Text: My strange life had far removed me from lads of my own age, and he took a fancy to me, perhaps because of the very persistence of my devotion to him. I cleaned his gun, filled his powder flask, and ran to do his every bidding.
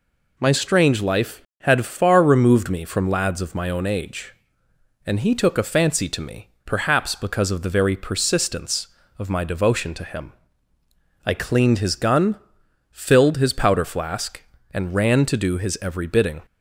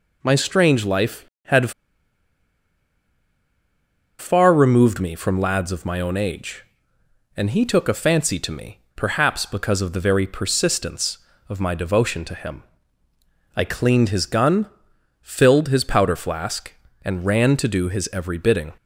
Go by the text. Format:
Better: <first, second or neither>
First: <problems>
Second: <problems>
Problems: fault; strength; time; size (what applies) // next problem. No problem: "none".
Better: first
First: none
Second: pauses between "had" and "far"; strong; at 1.7 s; 2.4 s long